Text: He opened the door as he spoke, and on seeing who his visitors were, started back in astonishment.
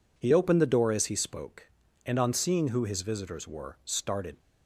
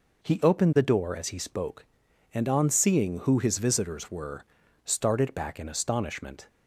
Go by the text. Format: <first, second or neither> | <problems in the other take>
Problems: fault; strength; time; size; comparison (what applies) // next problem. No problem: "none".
second | stops before "back in astonishment"; at 4.3 s